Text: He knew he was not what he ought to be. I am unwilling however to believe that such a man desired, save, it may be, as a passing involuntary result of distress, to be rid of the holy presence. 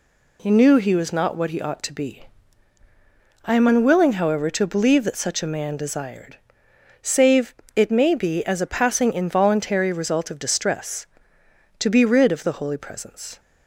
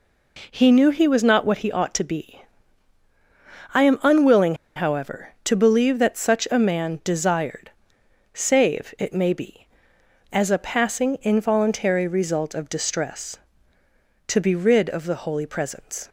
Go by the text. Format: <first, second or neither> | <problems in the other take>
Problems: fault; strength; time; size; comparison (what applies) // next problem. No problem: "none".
first | pauses between "unwilling" and "however"; slight; at 4.5 s; 0.20 s long